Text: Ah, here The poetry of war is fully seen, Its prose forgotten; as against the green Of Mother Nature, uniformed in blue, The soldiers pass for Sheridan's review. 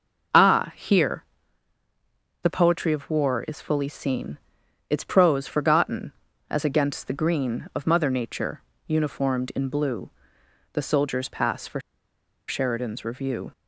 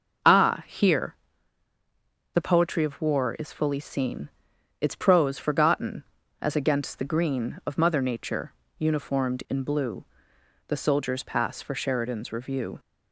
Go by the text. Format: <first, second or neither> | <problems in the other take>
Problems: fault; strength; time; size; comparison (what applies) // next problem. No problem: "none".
second | pauses between "here" and "The"; at 1.2 s; 1.1 s long; also in the second // pauses between "for" and "Sheridan's"; noticeable; at 11.8 s; 0.67 s long